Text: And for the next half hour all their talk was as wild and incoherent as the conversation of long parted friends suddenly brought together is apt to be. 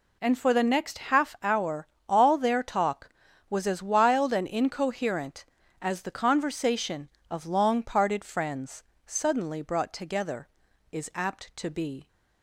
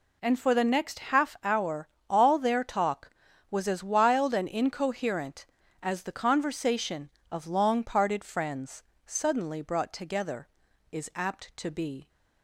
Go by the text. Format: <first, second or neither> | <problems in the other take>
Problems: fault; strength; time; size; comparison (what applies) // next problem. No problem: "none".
neither | pauses between "hour" and "all"; slight; the same in both // pauses between "friends" and "suddenly"; slight; the same in both